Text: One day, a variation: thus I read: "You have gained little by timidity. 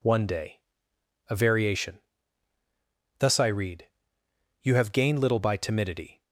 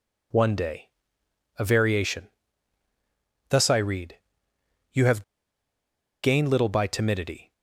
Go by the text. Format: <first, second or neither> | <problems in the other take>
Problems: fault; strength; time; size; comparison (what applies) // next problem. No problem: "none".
first | pauses between "have" and "gained"; at 5.2 s; 0.99 s long